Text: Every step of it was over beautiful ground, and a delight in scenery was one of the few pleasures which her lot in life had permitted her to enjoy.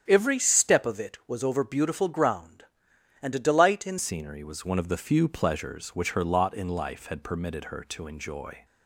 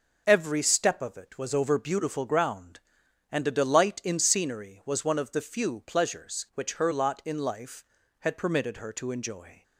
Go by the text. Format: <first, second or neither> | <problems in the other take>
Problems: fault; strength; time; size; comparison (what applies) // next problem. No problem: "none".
second | starts louder than the rest; strong; until 1.0 s; 9 dB; also in the second // changes voice at "scenery"; from 3.9 s on; 4.7 s long